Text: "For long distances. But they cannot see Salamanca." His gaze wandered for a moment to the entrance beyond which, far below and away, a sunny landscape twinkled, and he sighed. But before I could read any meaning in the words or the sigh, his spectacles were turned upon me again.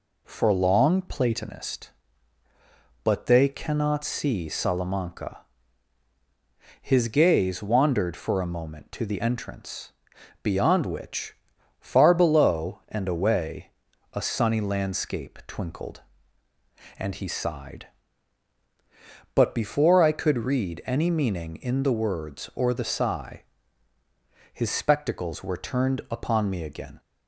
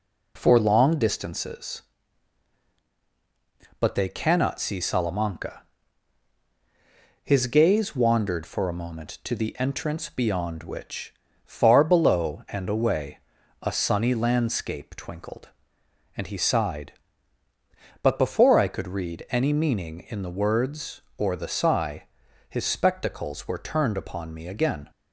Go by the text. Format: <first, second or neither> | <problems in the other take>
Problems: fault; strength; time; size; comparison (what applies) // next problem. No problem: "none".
second | says "platonist" for "distances"; at 1.0 s // pauses between "entrance" and "beyond"; noticeable; at 9.9 s; 0.50 s long